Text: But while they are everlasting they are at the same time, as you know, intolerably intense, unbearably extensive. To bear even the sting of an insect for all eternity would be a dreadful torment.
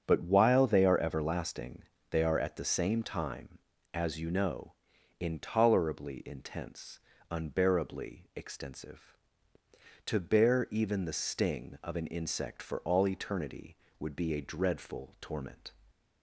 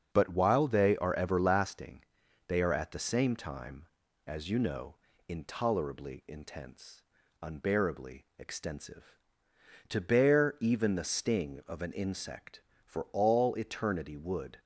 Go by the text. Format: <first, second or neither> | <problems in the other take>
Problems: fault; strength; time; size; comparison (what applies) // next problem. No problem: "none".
first | starts louder than the rest; until 1.1 s; 6.5 dB; strong in the first // pauses between "everlasting" and "they"; at 2.0 s; 0.44 s long; slight in the first // stops before "be a dreadful torment"; at 14.5 s